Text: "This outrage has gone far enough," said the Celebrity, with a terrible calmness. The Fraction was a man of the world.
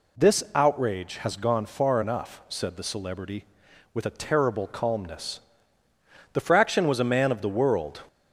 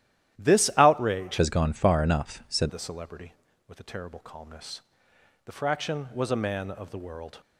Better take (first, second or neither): first